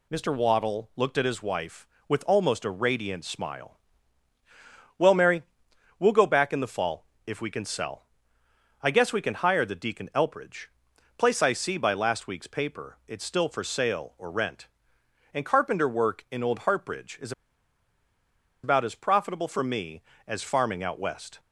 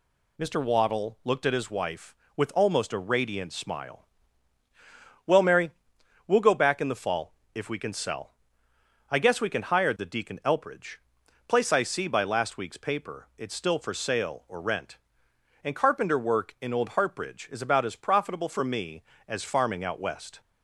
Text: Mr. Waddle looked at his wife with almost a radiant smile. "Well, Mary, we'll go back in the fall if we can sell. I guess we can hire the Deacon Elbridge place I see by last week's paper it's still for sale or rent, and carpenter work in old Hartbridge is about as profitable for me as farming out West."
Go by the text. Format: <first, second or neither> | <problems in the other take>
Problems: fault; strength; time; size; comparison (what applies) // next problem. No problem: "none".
second | pauses between "fall" and "if"; slight; at 7.0 s; 0.18 s long; slight in the second // pauses between "Elbridge" and "place"; noticeable; at 10.6 s; 0.50 s long; noticeable in the second // pauses between "is" and "about"; strong; at 17.3 s; 1.3 s long